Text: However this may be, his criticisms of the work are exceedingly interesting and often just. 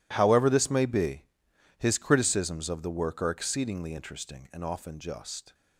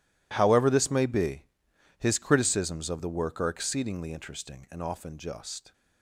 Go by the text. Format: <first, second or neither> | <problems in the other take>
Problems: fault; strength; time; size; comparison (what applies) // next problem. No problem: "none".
neither | none